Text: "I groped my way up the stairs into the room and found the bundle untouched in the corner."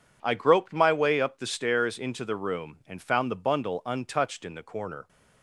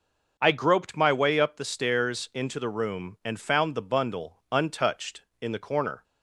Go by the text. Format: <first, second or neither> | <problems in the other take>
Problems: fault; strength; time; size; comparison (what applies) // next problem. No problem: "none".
neither | none